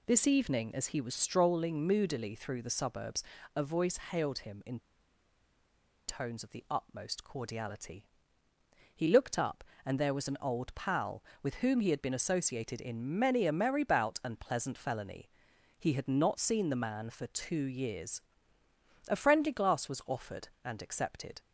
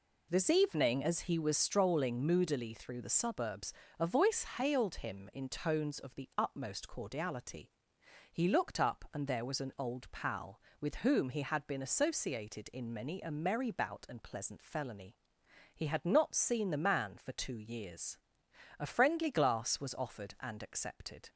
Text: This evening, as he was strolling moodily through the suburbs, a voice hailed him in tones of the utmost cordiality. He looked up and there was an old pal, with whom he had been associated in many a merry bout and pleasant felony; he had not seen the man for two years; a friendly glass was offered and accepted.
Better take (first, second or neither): second